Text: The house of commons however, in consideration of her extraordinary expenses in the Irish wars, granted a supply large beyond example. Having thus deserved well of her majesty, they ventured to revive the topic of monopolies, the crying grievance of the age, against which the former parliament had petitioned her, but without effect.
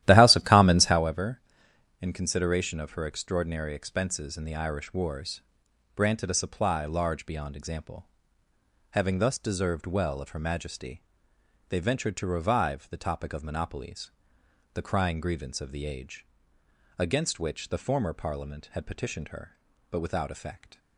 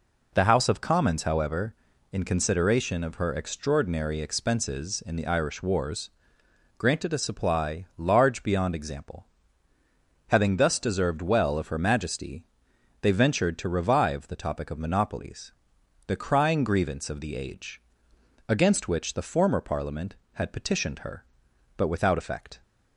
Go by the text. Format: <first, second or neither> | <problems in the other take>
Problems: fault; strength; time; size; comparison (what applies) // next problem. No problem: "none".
second | starts louder than the rest; strong; until 1.0 s; 13.5 dB